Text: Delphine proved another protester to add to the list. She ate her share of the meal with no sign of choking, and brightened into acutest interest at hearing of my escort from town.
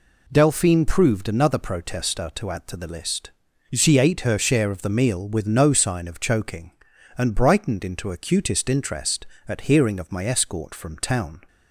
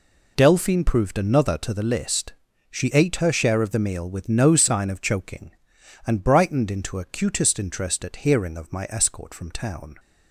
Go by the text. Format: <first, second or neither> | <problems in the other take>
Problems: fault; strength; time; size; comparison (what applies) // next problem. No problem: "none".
first | skips "protester to add"; at 1.5 s